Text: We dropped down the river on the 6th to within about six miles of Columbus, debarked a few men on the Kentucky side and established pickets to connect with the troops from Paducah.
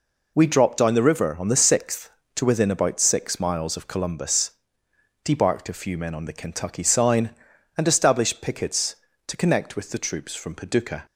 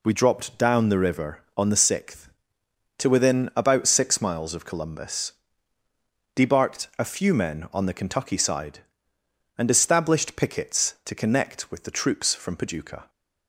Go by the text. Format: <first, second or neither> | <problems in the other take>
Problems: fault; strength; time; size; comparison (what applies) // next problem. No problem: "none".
second | says "sign" for "side"; at 6.8 s